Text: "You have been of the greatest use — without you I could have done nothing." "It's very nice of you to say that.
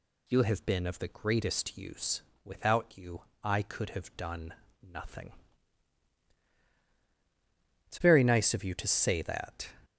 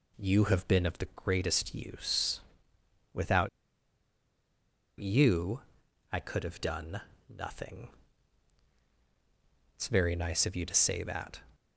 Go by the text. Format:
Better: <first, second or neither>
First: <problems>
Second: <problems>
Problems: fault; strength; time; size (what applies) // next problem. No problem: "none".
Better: first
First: pauses between "you" and "I"; slight; at 3.2 s; 0.22 s long // pauses between "done" and "nothing"; slight; at 4.5 s; 0.26 s long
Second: pauses between "without" and "you"; strong; at 3.4 s; 1.5 s long // pauses between "you" and "I"; noticeable; at 5.6 s; 0.50 s long // pauses between "done" and "nothing"; slight; at 7.0 s; 0.26 s long